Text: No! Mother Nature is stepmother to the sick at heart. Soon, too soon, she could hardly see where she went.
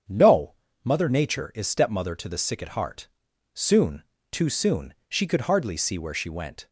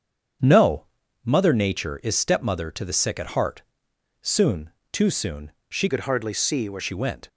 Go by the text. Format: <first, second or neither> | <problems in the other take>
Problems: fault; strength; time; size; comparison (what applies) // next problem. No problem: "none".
first | starts louder than the rest; strong; until 1.7 s; 7.5 dB; strong in the first // changes voice from "could" to "where"; from 5.8 to 6.8 s; 1.0 s long